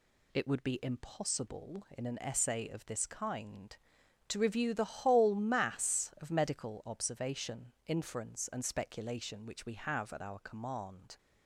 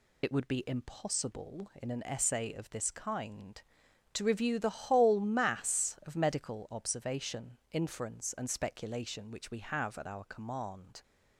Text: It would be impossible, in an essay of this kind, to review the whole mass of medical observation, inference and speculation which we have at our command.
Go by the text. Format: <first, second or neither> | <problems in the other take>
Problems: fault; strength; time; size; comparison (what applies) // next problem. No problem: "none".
first | loses the start of "It"; at 0.2 s; 55 ms